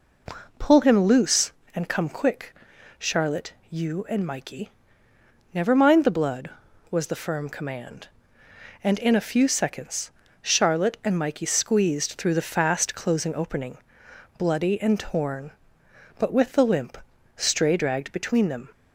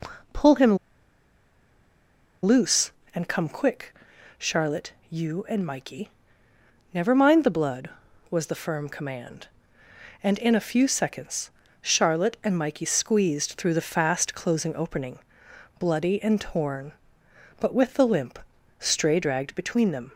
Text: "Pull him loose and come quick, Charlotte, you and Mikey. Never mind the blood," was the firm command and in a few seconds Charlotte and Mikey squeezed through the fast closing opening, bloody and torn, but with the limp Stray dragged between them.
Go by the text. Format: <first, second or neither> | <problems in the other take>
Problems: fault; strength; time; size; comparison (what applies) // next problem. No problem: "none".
first | pauses between "him" and "loose"; strong; at 0.7 s; 1.6 s long // pauses between "seconds" and "Charlotte"; slight; at 11.5 s; 0.30 s long; slight in the first // pauses between "limp" and "Stray"; at 18.3 s; 0.40 s long; also in the first